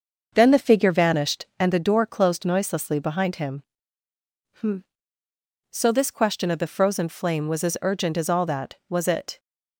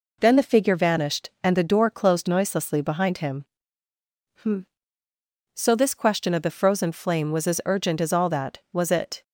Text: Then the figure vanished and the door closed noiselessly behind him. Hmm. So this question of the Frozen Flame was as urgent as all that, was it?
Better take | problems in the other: second | starts louder than the rest; until 1.7 s; 6.5 dB

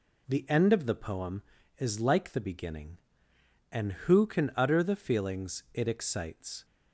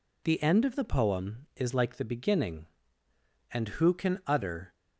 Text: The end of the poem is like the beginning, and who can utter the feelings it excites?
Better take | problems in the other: first | stops before "the feelings it excites"; at 4.7 s

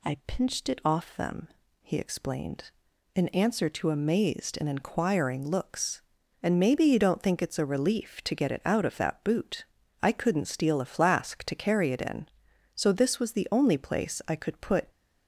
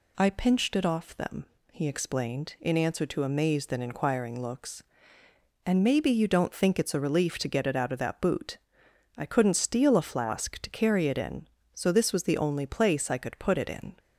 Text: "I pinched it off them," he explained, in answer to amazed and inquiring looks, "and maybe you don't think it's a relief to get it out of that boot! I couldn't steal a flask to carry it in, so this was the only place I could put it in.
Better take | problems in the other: second | stops before "it in"; at 14.8 s

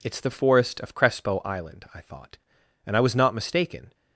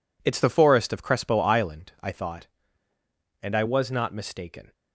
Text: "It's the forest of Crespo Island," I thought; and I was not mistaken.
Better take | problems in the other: neither | none

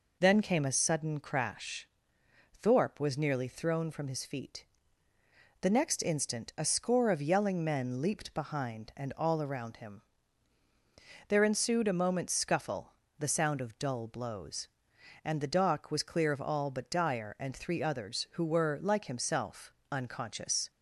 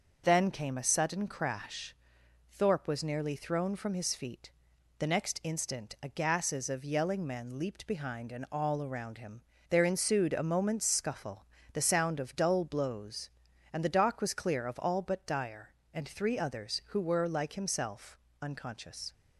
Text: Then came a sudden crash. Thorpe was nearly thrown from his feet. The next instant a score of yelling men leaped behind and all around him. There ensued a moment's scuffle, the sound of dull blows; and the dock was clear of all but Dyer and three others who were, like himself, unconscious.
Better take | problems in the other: first | starts louder than the rest; until 1.2 s; 6.5 dB // says "gases" for "score"; at 6.0 s

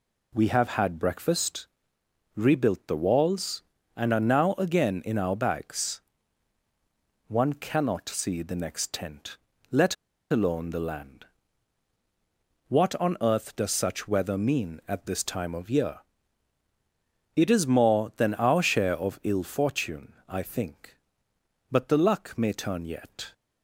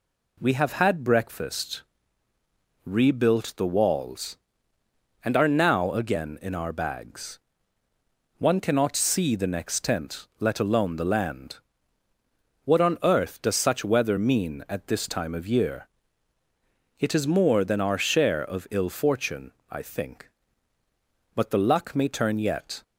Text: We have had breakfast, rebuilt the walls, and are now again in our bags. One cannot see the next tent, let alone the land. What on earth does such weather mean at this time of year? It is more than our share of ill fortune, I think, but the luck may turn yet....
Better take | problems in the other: second | pauses between "let" and "alone"; slight; at 9.9 s; 0.35 s long

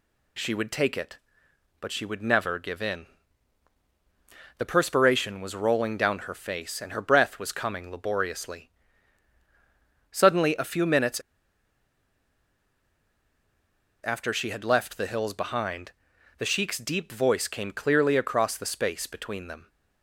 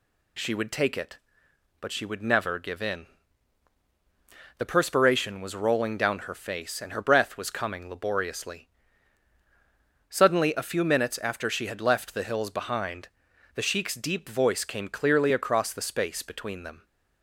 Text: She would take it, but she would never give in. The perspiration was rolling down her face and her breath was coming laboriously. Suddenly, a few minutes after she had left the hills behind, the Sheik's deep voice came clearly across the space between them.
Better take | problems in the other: second | pauses between "minutes" and "after"; strong; at 11.1 s; 2.8 s long

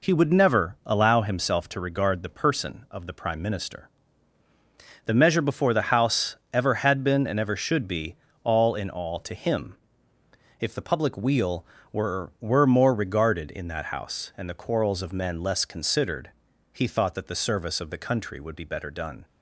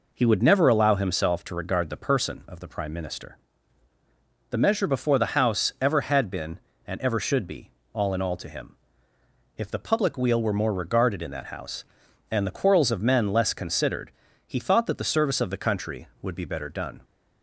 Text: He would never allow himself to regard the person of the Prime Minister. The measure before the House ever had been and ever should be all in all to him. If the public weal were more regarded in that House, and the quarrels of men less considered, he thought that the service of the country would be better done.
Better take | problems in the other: second | pauses between "House" and "ever"; slight; at 6.3 s; 0.16 s long // pauses between "be" and "all"; slight; at 8.1 s; 0.28 s long; slight in the second // says "were" twice; at 12.4 s

